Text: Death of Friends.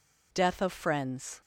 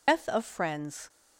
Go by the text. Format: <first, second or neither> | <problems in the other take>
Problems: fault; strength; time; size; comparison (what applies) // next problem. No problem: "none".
first | loses the start of "Death"; at 0.0 s; 95 ms